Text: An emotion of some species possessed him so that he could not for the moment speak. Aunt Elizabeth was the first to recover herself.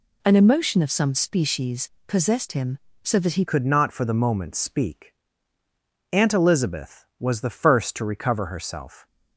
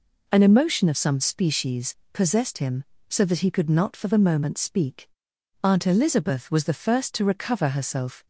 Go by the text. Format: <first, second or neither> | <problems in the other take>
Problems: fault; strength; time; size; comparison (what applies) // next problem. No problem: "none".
second | pauses between "species" and "possessed"; slight; at 1.8 s; 0.18 s long; slight in the second // changes voice at "could"; from 3.4 s on; 5.6 s long